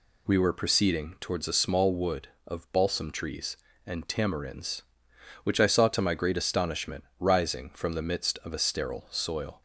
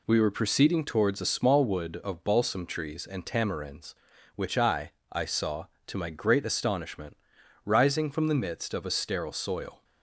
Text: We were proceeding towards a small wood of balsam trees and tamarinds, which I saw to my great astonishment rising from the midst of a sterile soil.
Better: first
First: pauses between "astonishment" and "rising"; slight; at 7.0 s; 0.16 s long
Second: says "I" twice; at 5.1 s // pauses between "astonishment" and "rising"; noticeable; at 7.1 s; 0.48 s long

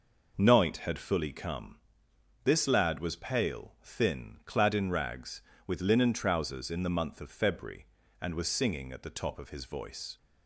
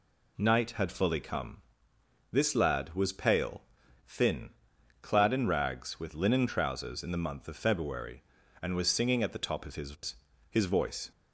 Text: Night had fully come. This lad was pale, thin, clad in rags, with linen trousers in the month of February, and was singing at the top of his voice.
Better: first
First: none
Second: says "his" twice; at 10.4 s

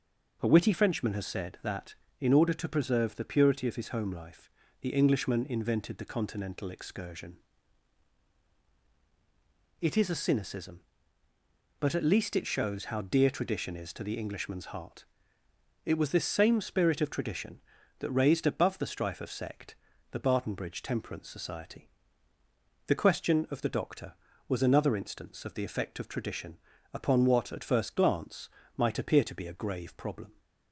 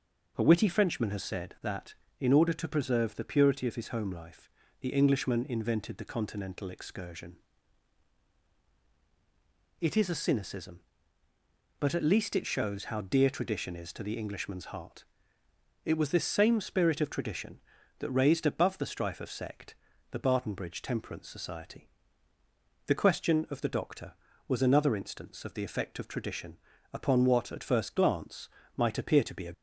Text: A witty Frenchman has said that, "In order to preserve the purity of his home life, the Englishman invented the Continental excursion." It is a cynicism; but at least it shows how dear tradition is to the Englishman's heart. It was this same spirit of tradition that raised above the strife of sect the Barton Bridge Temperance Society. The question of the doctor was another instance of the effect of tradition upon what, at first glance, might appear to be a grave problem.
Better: first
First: pauses between "sect" and "the"; at 19.7 s; 0.38 s long // pauses between "tradition" and "upon"; slight; at 26.5 s; 0.36 s long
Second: pauses between "sect" and "the"; at 19.7 s; 0.38 s long // pauses between "tradition" and "upon"; slight; at 26.5 s; 0.36 s long // stops before "grave problem"; at 29.5 s

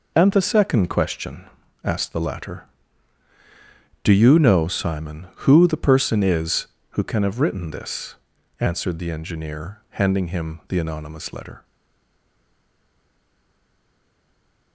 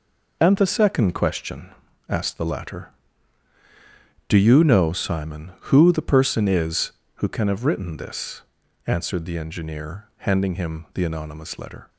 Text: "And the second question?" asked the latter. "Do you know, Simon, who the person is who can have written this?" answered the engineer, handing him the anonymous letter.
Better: second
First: stays silent after the last word; strong; from 11.6 s on; 3.1 s long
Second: none

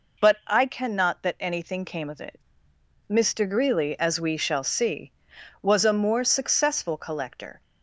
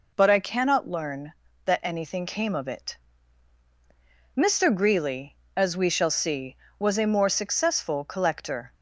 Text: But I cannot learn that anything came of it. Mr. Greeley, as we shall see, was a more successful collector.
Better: second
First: skips "learn"; at 1.2 s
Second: none

